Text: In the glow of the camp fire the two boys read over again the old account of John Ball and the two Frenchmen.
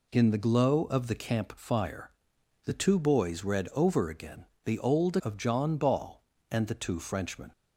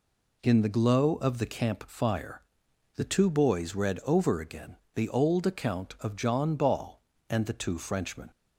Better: second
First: pauses between "fire" and "the"; noticeable; at 2.1 s; 0.54 s long // pauses between "again" and "the"; slight; at 4.4 s; 0.18 s long // skips "account"; at 5.1 s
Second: pauses between "fire" and "the"; noticeable; at 2.4 s; 0.54 s long // pauses between "again" and "the"; slight; at 4.7 s; 0.17 s long

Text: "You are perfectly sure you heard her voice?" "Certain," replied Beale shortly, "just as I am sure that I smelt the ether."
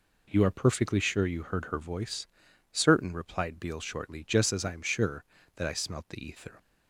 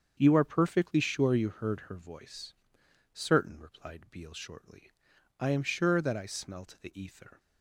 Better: first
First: none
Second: starts louder than the rest; strong; until 1.2 s; 7 dB // skips "just as"; at 5.1 s

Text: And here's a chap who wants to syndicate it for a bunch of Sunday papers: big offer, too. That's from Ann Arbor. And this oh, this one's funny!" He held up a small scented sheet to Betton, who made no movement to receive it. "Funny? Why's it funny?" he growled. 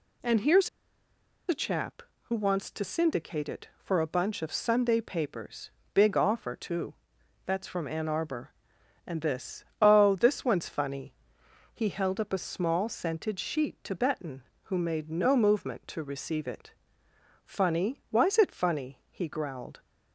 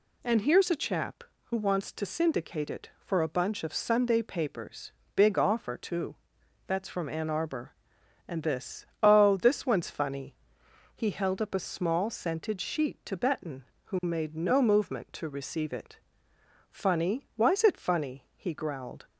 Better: second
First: pauses between "here's" and "a"; noticeable; at 0.6 s; 0.80 s long // pauses between "this" and "oh"; slight; at 9.6 s; 0.16 s long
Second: pauses between "this" and "oh"; slight; at 8.8 s; 0.16 s long

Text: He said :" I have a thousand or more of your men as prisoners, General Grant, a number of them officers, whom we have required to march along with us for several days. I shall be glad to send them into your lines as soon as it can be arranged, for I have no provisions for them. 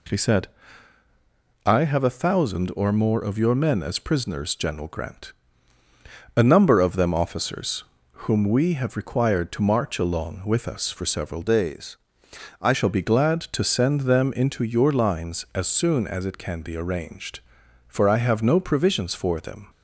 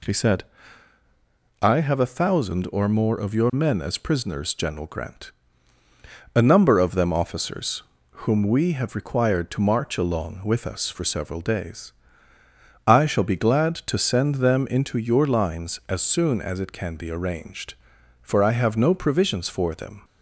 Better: second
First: changes voice from "days" to "I"; from 11.4 to 12.7 s; 1.3 s long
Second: none

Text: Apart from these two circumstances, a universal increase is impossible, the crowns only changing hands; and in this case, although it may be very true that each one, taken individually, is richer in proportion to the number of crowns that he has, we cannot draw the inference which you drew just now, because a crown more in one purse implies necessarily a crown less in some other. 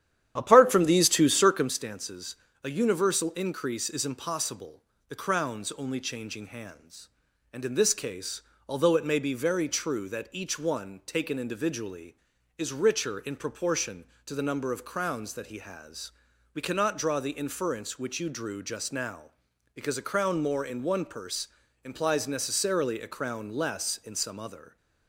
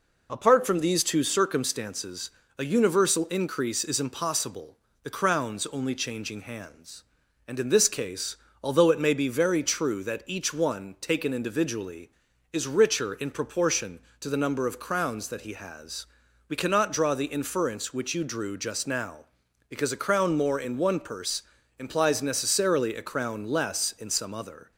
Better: second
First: starts louder than the rest; strong; until 1.7 s; 10.5 dB // pauses between "purse" and "implies"; slight; at 21.4 s; 0.34 s long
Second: pauses between "purse" and "implies"; slight; at 21.4 s; 0.34 s long

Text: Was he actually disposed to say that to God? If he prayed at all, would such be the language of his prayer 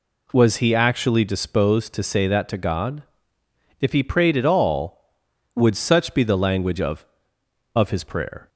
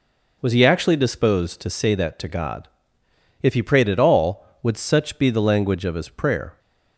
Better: second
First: says "of" twice; at 7.7 s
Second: none

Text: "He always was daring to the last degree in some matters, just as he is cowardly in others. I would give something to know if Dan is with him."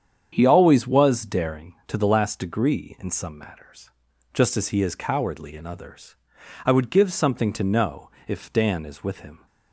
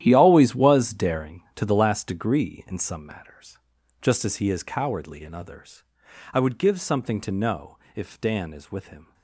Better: first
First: starts louder than the rest; strong; until 1.3 s; 8 dB // pauses between "know" and "if"; slight; at 8.0 s; 0.16 s long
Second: gets quieter; strong; throughout; 13 dB // starts louder than the rest; strong; until 1.0 s; 11.5 dB // pauses between "know" and "if"; slight; at 7.7 s; 0.16 s long

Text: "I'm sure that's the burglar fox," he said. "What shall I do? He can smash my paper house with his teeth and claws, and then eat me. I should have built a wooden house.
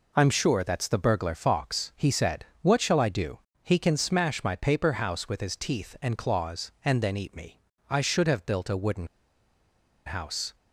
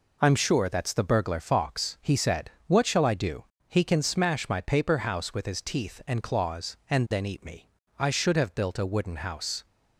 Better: second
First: pauses between "wooden" and "house"; at 9.0 s; 0.99 s long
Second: none

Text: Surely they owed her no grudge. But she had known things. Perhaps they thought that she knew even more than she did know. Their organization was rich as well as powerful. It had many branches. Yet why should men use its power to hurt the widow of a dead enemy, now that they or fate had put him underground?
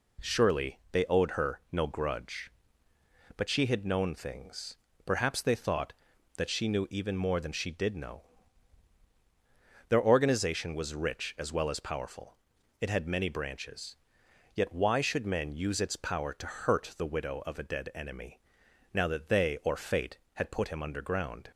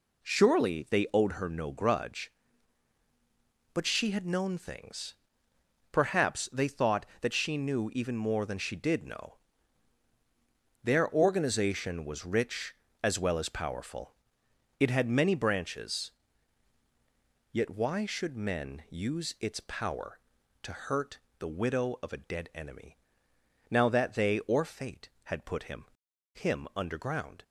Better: first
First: none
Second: pauses between "hurt" and "the"; slight; at 21.1 s; 0.20 s long // says "him" twice; at 26.3 s

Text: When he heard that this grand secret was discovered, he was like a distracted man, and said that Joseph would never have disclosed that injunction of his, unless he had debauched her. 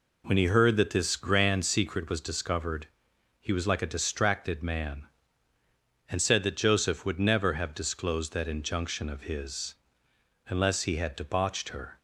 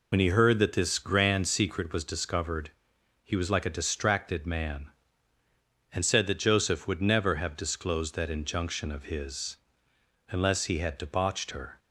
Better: first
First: none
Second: loses the start of "When"; at 0.1 s; 55 ms

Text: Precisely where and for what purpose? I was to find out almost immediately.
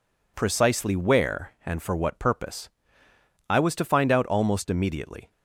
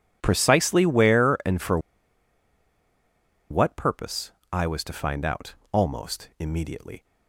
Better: first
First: none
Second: pauses between "for" and "what"; strong; at 1.7 s; 1.7 s long // pauses between "out" and "almost"; slight; at 5.5 s; 0.18 s long

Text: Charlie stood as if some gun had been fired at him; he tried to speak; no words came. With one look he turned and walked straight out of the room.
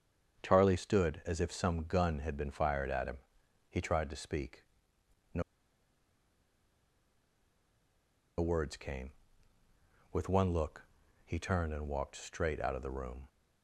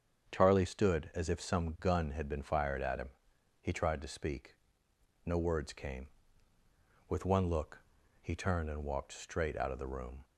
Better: second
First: starts louder than the rest; strong; until 1.4 s; 7.5 dB // pauses between "no" and "words"; strong; at 5.4 s; 2.9 s long // pauses between "look" and "he"; at 10.8 s; 0.42 s long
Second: starts louder than the rest; strong; until 1.3 s; 7.5 dB // pauses between "look" and "he"; at 7.8 s; 0.42 s long

